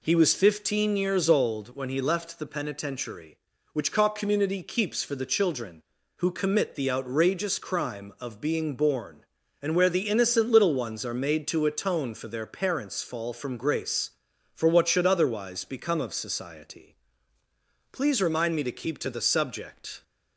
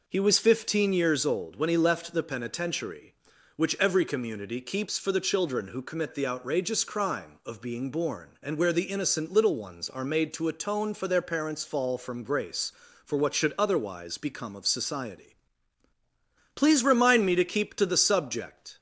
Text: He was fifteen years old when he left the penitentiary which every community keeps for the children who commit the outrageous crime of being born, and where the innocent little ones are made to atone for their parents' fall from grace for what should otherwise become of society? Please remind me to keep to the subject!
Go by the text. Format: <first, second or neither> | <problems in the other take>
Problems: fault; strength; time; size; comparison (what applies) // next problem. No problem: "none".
second | says "cock" for "every"; at 3.9 s